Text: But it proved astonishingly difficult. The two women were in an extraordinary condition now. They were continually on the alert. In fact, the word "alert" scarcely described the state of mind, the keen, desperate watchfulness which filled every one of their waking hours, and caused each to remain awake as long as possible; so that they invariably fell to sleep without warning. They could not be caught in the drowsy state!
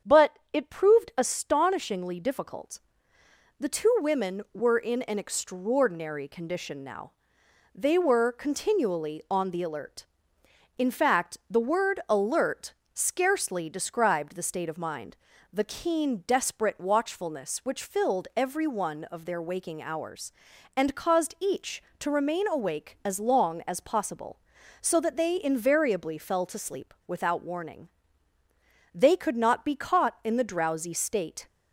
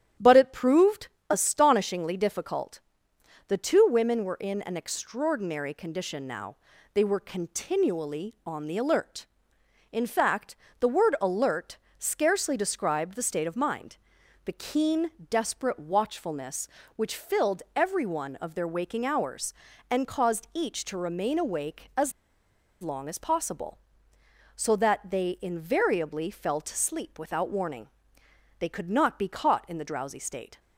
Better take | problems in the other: first | starts louder than the rest; strong; until 1.4 s; 10 dB; strong in the first // pauses between "proved" and "astonishingly"; slight; at 1.0 s; 0.24 s long // pauses between "alert" and "scarcely"; slight; at 11.7 s; 0.22 s long; slight in the first // pauses between "as" and "long"; noticeable; at 22.1 s; 0.69 s long

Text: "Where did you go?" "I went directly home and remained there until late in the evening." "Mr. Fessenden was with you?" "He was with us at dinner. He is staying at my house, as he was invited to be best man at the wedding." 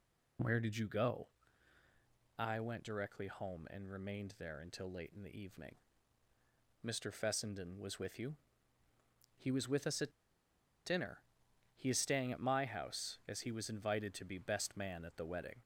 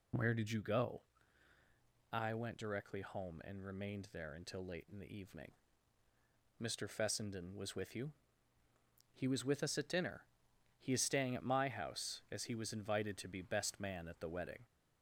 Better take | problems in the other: second | pauses between "at" and "dinner"; noticeable; at 10.1 s; 0.73 s long

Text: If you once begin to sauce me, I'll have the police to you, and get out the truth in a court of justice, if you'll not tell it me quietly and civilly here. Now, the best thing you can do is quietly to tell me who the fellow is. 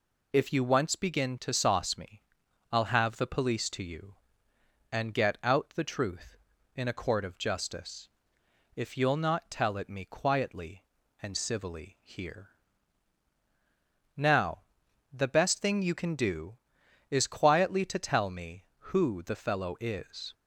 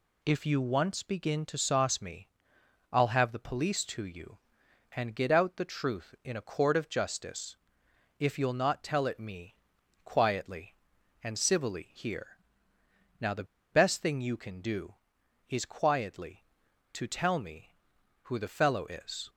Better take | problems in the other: first | pauses between "me" and "quietly"; noticeable; at 9.5 s; 0.48 s long // pauses between "the" and "best"; slight; at 13.4 s; 0.28 s long

